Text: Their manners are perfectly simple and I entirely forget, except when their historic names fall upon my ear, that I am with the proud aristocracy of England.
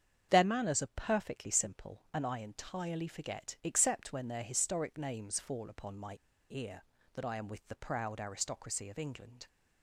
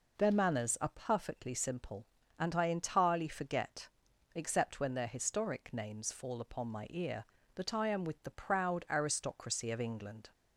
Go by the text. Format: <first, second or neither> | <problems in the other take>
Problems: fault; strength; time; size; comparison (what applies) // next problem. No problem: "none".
second | starts louder than the rest; strong; until 1.3 s; 8 dB // pauses between "my" and "ear"; at 6.1 s; 0.37 s long